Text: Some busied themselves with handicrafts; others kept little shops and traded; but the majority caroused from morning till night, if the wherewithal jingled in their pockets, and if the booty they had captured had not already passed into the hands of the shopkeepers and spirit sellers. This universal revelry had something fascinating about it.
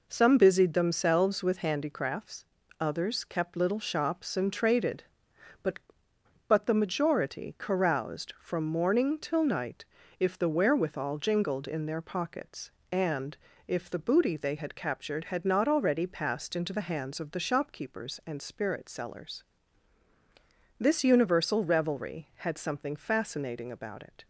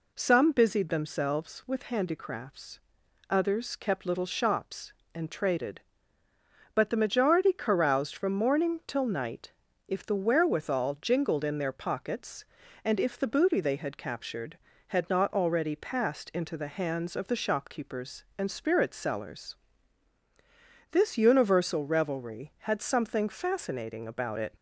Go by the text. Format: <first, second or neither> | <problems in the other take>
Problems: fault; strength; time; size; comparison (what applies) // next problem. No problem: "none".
second | says "but" twice; at 6.4 s // pauses between "and" and "if"; slight; at 13.3 s; 0.30 s long